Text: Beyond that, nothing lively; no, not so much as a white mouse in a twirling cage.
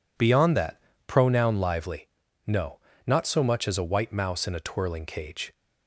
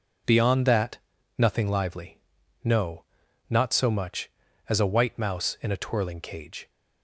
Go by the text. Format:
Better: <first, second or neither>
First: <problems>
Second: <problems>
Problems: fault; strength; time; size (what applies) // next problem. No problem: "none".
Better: second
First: says "pronoun" for "nothing"; at 1.0 s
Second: none